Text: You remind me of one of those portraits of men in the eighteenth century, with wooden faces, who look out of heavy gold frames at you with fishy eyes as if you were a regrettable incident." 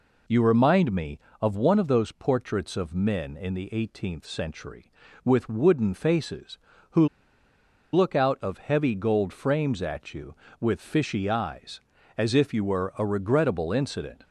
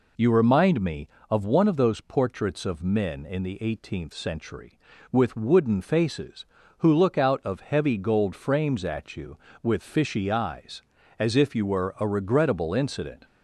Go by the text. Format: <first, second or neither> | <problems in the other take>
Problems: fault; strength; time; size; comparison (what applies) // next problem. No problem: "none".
second | pauses between "who" and "look"; noticeable; at 7.0 s; 0.86 s long